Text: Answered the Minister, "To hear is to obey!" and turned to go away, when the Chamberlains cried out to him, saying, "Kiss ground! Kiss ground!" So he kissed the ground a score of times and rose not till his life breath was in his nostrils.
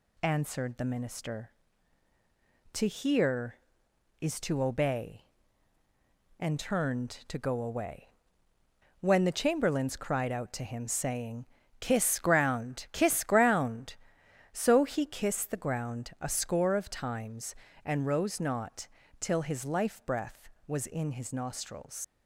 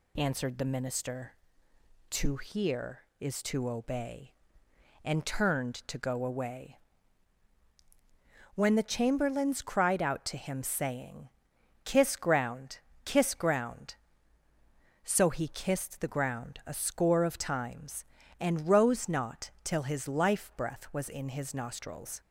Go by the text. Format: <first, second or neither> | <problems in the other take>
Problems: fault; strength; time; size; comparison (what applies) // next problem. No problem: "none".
second | pauses between "not" and "till"; slight; at 18.8 s; 0.32 s long // leaves "nostrils" unfinished; at 22.0 s; 95 ms